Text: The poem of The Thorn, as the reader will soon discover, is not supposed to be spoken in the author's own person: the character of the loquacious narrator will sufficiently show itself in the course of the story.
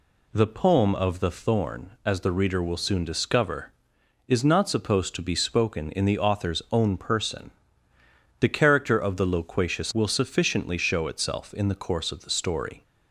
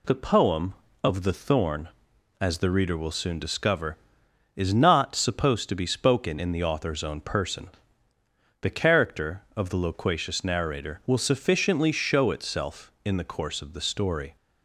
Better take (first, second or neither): second